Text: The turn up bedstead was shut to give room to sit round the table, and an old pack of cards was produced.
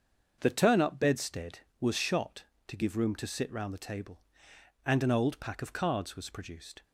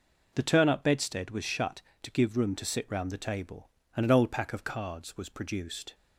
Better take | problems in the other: second | starts louder than the rest; until 1.4 s; 6.5 dB // says "shot" for "shut"; at 1.9 s

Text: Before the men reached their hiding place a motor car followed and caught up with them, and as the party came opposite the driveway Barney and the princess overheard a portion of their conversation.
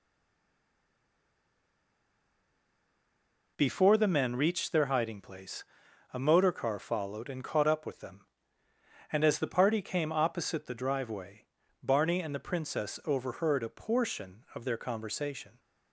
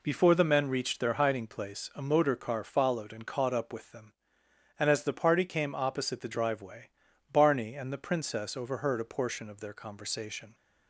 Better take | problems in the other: second | stays silent before the first word; strong; until 3.5 s; 3.5 s long // pauses between "place" and "a"; noticeable; at 5.6 s; 0.50 s long // pauses between "driveway" and "Barney"; slight; at 11.4 s; 0.36 s long; also in the second

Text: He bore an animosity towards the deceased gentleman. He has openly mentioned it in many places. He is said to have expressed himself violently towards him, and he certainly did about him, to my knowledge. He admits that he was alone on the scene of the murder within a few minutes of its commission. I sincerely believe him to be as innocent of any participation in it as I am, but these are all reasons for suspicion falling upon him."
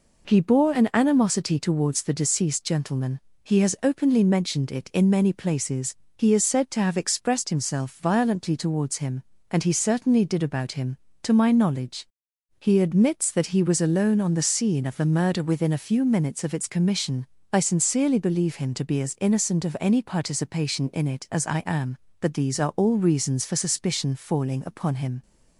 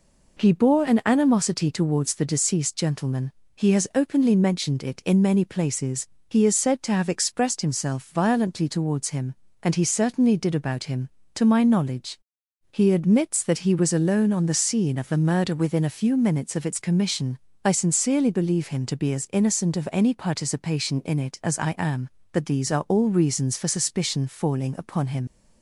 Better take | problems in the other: first | leaves "him" unfinished; at 25.2 s; 65 ms

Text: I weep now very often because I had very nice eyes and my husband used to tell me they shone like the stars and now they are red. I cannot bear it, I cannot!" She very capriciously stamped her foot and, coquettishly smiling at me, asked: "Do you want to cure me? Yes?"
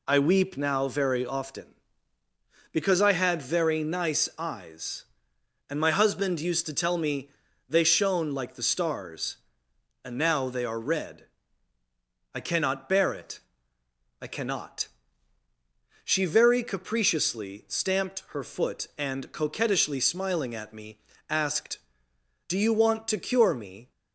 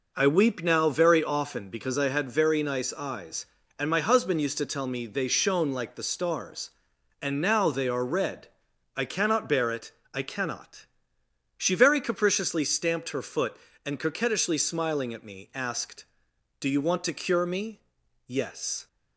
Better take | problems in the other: second | pauses between "me" and "they"; at 7.2 s; 0.40 s long // stops before "Yes"; at 23.9 s

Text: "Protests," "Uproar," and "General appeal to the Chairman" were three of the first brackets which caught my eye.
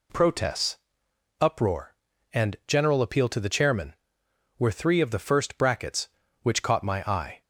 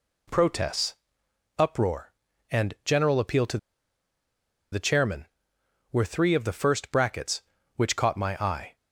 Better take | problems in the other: first | pauses between "to" and "the"; at 3.5 s; 1.1 s long

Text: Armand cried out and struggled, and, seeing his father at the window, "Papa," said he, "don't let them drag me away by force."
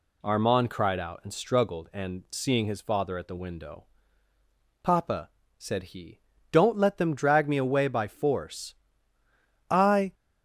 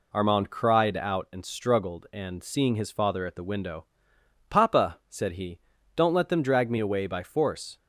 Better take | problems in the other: second | goes on to say "I"; slight; from 9.6 s on; 0.44 s long

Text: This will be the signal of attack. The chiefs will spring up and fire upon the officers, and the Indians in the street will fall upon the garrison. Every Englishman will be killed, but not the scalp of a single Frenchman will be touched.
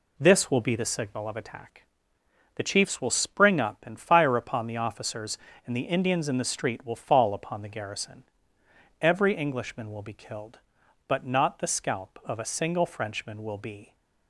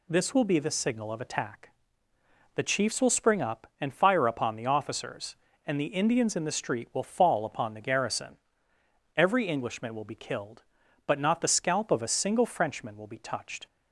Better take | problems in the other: second | stops before "touched"; at 13.9 s

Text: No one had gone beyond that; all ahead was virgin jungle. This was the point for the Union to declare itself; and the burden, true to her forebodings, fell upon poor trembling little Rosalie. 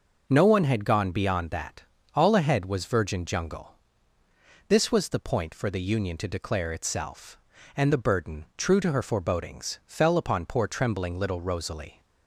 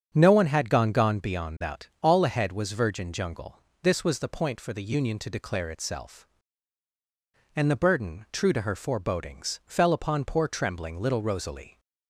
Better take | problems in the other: first | starts louder than the rest; strong; until 1.1 s; 7 dB // says "gone" twice; at 0.9 s

